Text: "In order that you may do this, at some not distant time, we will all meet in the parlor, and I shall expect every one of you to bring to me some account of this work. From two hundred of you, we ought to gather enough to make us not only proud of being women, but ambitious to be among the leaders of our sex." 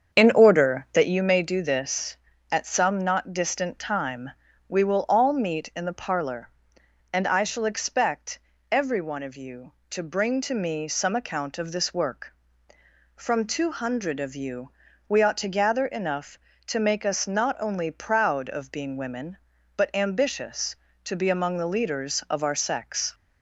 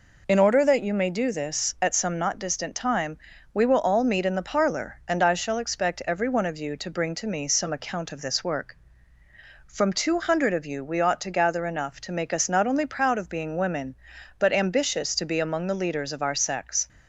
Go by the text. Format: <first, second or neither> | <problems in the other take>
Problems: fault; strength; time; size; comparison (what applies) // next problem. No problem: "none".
second | starts louder than the rest; strong; until 1.3 s; 7.5 dB // pauses between "expect" and "every"; slight; at 8.3 s; 0.32 s long